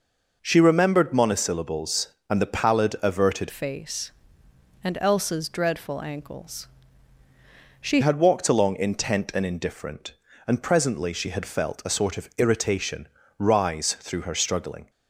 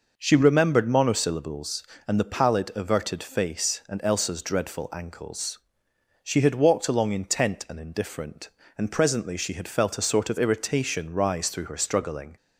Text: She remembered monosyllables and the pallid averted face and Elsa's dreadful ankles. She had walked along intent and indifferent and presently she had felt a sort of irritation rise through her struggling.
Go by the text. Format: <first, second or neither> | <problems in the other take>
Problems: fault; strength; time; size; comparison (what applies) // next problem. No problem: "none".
second | changes voice from "face" to "She"; from 3.5 to 8.0 s; 4.5 s long // pauses between "irritation" and "rise"; slight; at 13.0 s; 0.30 s long